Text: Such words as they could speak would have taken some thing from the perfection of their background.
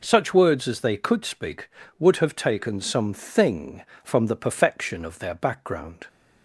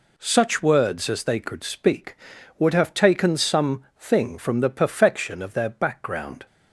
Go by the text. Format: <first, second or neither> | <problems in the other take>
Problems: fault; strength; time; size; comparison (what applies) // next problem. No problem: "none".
neither | none